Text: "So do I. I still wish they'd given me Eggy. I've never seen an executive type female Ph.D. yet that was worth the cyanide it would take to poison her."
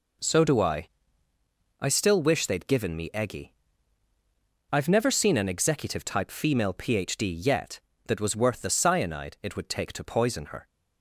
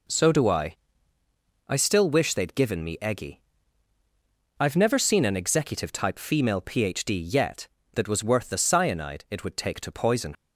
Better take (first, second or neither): first